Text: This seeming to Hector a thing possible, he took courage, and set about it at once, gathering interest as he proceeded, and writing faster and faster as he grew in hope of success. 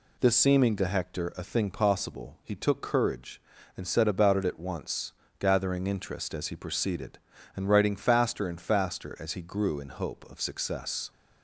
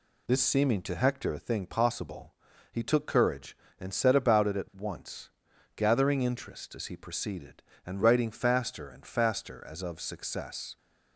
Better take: first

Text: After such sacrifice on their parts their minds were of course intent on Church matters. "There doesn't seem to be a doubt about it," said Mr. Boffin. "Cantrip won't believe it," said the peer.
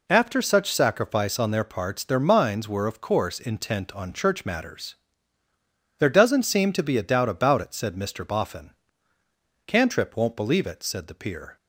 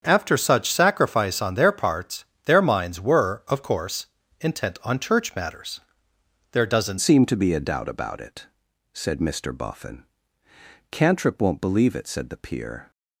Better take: first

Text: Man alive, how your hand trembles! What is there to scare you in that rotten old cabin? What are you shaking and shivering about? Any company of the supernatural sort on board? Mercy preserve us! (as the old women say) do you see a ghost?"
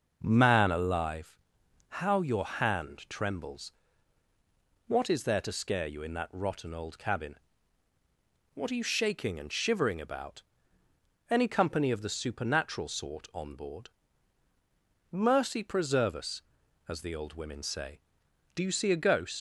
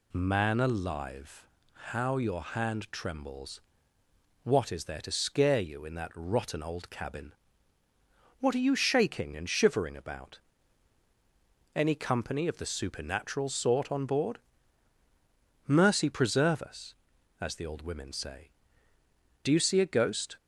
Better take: second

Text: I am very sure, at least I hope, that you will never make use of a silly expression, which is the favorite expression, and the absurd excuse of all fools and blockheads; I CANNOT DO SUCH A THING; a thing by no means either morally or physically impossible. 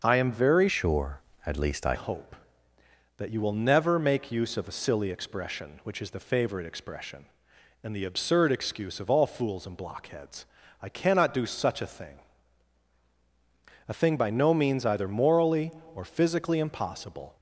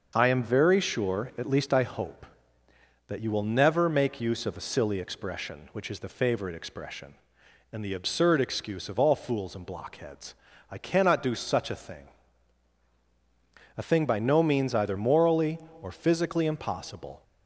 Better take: second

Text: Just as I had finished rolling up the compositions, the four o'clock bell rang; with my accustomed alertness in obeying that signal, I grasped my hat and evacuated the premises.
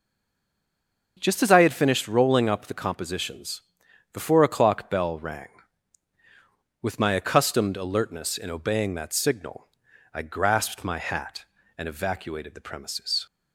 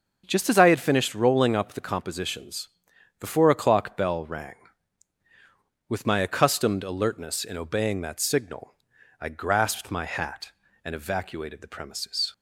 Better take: second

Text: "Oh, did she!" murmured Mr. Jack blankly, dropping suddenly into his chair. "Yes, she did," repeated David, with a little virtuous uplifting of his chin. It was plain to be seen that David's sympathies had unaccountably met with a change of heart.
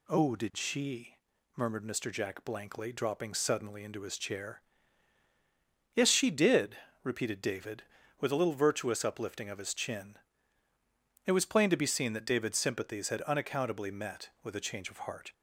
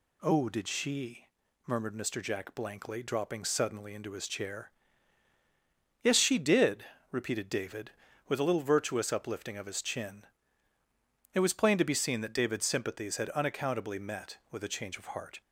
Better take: neither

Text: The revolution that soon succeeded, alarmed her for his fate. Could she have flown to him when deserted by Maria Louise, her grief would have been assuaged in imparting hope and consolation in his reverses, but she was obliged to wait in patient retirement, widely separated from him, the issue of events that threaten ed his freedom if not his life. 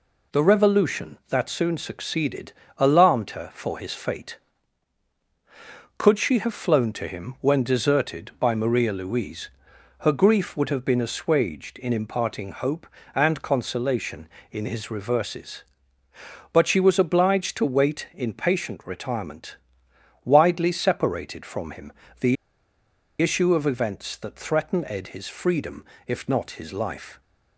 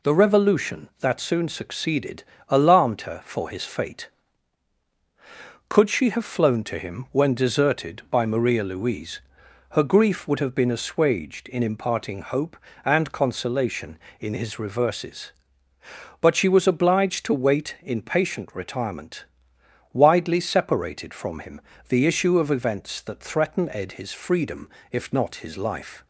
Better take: second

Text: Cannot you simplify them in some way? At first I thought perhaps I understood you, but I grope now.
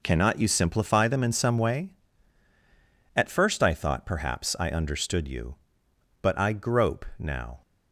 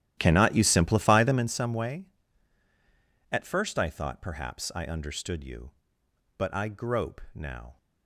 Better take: first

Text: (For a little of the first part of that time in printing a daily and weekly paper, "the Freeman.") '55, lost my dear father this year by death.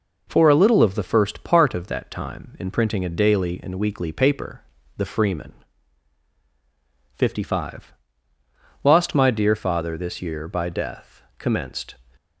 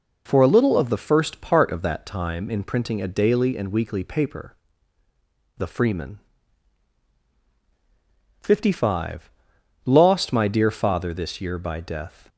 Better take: second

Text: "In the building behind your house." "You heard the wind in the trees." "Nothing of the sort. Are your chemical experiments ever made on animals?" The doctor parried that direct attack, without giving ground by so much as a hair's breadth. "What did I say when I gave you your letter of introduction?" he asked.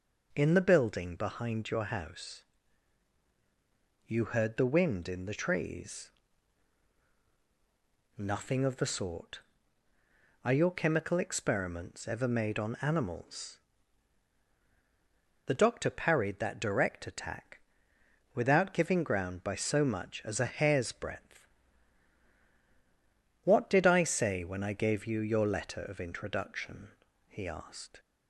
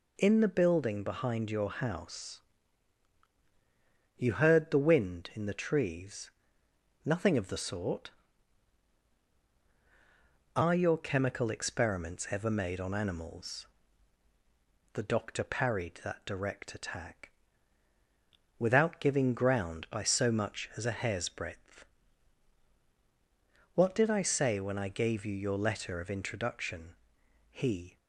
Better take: first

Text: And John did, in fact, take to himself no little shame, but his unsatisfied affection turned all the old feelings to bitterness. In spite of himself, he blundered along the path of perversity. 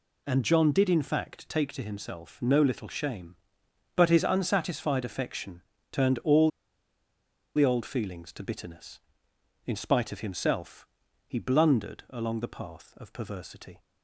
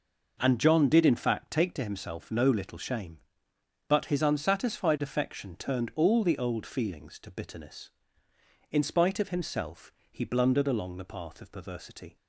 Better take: second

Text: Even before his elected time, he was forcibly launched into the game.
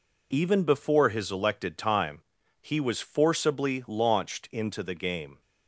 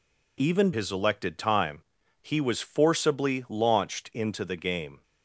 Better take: first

